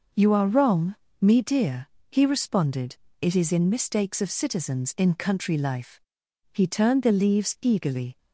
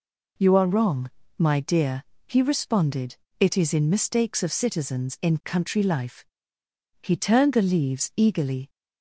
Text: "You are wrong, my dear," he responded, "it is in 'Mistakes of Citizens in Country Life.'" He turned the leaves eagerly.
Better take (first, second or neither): second